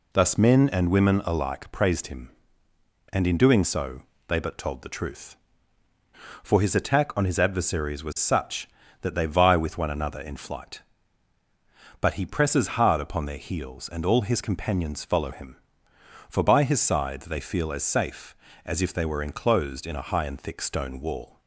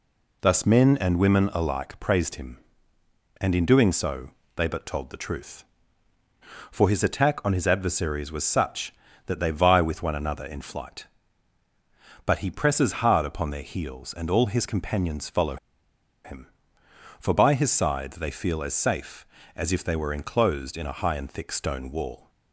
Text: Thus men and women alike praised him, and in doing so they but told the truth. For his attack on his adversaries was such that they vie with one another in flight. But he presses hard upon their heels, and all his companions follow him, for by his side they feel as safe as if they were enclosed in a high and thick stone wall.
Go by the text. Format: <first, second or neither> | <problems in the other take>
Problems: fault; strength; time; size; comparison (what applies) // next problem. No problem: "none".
first | pauses between "so" and "they"; slight; at 4.2 s; 0.26 s long; slight in the first // pauses between "follow" and "him"; noticeable; at 15.5 s; 0.68 s long